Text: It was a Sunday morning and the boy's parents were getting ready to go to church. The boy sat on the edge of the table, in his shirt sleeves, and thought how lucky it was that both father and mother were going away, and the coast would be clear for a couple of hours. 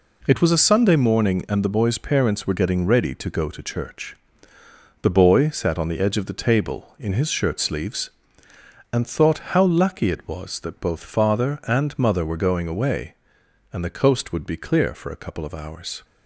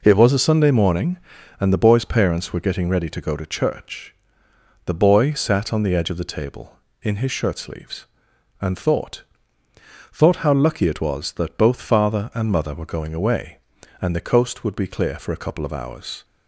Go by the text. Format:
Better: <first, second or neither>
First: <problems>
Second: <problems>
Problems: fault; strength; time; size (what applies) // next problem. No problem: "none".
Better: first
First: none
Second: says "thought" twice; at 10.1 s